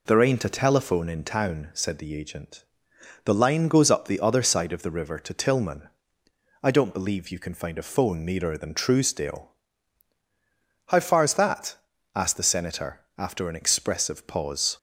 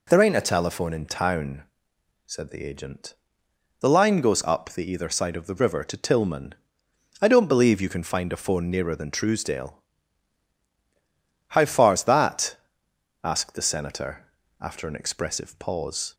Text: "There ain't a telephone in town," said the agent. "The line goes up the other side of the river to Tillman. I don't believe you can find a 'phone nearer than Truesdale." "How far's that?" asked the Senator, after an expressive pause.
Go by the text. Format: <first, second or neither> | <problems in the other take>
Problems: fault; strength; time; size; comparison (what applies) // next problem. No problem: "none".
first | says "either" for "other"; at 4.9 s